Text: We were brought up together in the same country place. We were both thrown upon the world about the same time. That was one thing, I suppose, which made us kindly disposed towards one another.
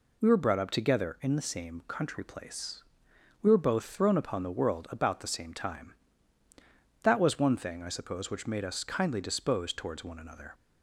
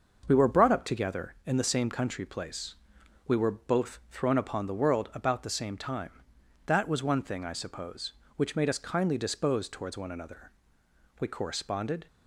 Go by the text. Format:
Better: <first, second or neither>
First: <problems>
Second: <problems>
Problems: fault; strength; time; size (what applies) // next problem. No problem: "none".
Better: first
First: none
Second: starts louder than the rest; until 1.2 s; 6 dB // goes on to say "We corresponded"; noticeable; from 11.1 s on; 0.88 s long